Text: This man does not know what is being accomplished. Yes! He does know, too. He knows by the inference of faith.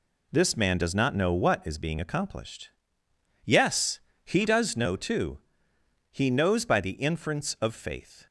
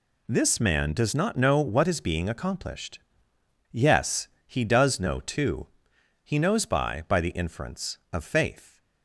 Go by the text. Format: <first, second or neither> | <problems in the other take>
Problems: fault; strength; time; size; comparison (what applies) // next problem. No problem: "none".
first | says "by" twice; at 7.0 s